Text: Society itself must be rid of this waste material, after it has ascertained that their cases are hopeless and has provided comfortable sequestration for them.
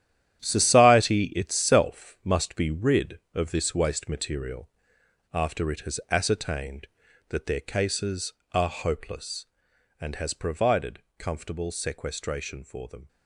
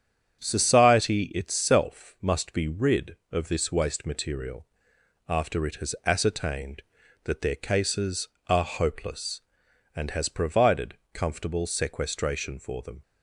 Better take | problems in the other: second | gets quieter; strong; throughout; 11 dB // starts louder than the rest; strong; until 1.5 s; 11 dB; strong in the second // pauses between "provided" and "comfortable"; slight; at 11.0 s; 0.16 s long; slight in the second

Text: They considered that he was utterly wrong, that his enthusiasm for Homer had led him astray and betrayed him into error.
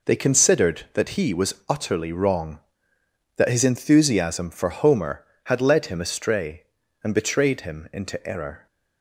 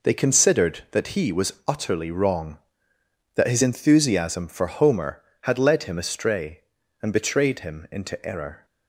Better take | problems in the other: neither | none

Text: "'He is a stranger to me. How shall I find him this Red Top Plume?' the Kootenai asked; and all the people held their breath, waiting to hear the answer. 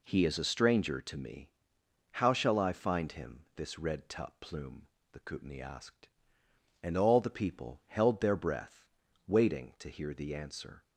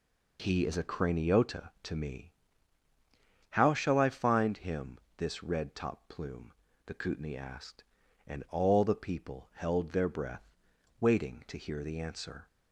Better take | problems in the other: first | says "craniota" for "stranger"; at 0.8 s // pauses between "him" and "this"; slight; at 4.9 s; 0.22 s long

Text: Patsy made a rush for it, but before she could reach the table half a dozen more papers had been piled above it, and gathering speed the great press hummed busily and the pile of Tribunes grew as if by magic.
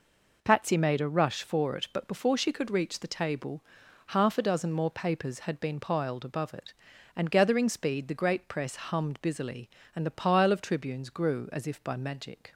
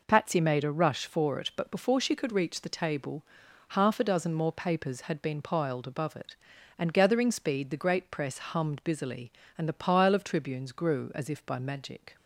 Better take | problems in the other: neither | pauses between "table" and "half"; the same in both

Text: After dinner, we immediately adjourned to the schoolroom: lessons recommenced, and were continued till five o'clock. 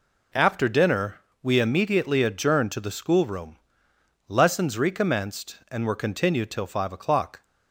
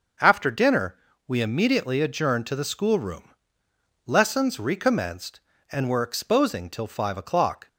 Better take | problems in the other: first | starts louder than the rest; noticeable; until 1.5 s; 6 dB // says "exposing" for "continued"; at 6.0 s

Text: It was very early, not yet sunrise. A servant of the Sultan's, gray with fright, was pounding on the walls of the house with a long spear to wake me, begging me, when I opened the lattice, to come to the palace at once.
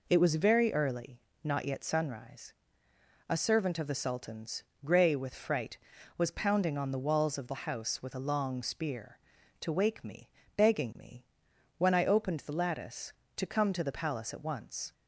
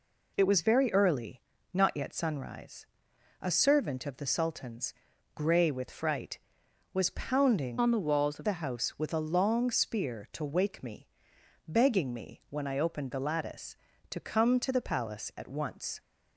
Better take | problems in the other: first | changes voice from "on" to "of"; from 7.7 to 8.4 s; 0.7 s long

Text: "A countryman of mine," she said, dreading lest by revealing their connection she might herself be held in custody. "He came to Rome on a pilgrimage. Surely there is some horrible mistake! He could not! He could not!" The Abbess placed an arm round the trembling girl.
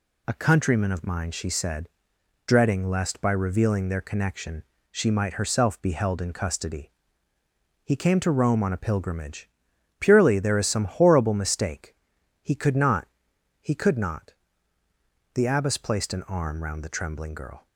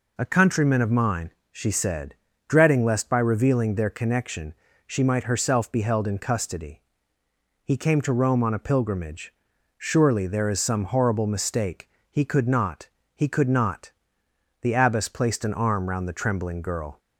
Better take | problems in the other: second | pauses between "connection" and "she"; slight; at 4.6 s; 0.28 s long; slight in the second // says "Purely" for "Surely"; at 9.9 s

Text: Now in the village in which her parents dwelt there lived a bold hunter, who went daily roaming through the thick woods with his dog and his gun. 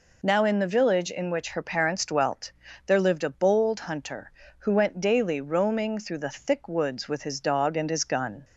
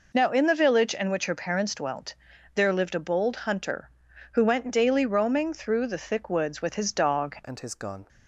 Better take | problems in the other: first | pauses between "dwelt" and "there"; at 2.1 s; 0.42 s long; slight in the first // changes voice at "and"; from 7.4 s on; 0.6 s long

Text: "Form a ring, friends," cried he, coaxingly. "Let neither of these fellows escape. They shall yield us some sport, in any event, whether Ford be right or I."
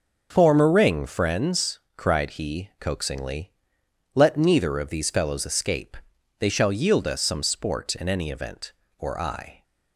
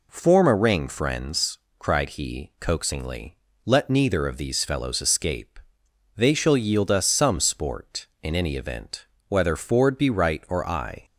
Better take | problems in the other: second | starts louder than the rest; until 1.3 s; 6.5 dB // skips "whether Ford be right"; at 8.8 s

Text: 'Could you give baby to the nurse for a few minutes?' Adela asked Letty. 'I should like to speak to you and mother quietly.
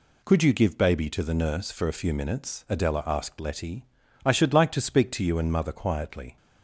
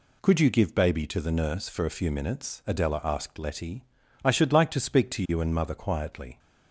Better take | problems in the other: neither | none

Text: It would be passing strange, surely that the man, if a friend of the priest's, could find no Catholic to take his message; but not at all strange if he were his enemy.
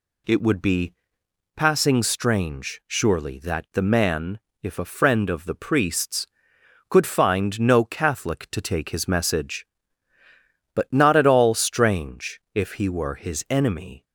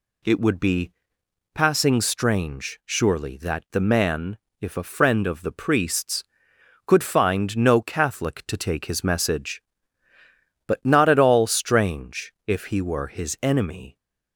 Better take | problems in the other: neither | pauses between "be" and "passing"; noticeable; the same in both

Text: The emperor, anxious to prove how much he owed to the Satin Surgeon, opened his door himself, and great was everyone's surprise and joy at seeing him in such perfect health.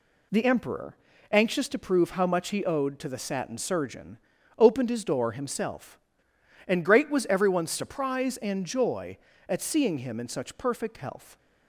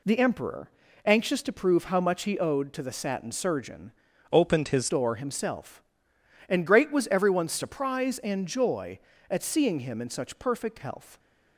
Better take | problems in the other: first | changes voice from "opened" to "his"; from 4.3 to 4.8 s; 0.5 s long

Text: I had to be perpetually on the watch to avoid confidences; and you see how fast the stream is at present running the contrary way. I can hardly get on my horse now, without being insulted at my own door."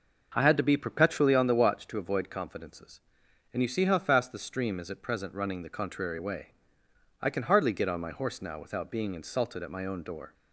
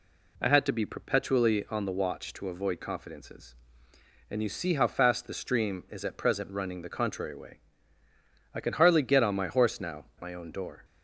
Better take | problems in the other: first | skips "without being insulted at"; at 10.1 s

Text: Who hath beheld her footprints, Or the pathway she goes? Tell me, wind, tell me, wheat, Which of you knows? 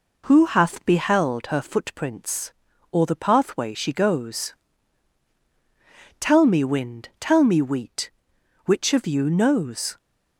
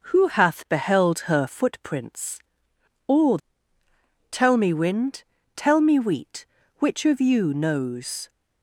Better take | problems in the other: first | skips "the pathway she goes"; at 3.8 s

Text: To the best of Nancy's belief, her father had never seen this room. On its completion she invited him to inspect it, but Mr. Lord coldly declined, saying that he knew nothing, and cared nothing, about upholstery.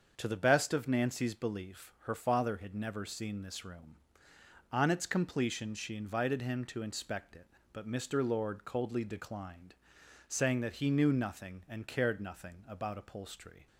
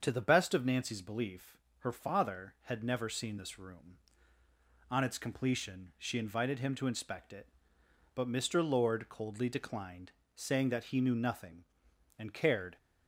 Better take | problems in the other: first | starts louder than the rest; until 1.0 s; 7 dB; also in the first // stops before "nothing about upholstery"; at 12.7 s

